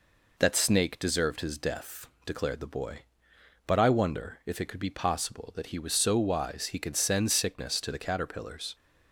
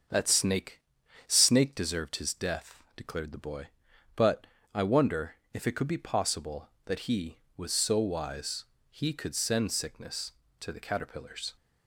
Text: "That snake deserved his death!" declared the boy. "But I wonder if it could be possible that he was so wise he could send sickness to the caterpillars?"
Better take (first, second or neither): first